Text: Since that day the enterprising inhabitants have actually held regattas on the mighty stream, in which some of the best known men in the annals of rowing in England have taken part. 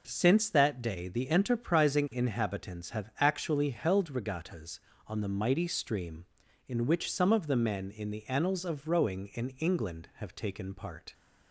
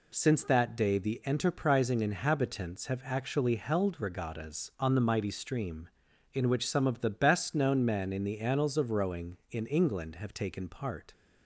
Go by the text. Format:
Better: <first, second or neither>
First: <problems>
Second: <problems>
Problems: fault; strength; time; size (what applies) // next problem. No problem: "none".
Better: second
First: skips "best known"; at 7.5 s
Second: none